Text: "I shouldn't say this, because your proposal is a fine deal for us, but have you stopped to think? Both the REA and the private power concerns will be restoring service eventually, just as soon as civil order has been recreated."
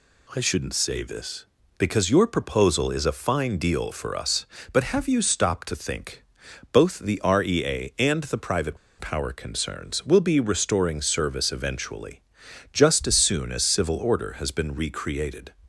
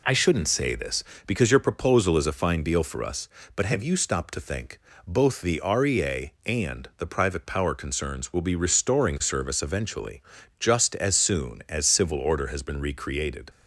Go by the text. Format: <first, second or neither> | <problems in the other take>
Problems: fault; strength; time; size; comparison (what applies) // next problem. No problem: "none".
second | pauses between "private" and "power"; slight; at 8.7 s; 0.22 s long